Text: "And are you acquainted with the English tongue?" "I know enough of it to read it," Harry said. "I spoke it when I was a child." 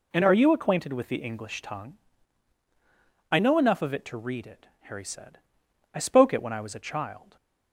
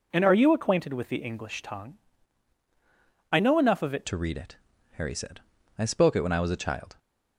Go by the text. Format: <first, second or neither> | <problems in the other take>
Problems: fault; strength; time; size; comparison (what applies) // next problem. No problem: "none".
first | changes voice at "to"; from 4.0 s on; 2.9 s long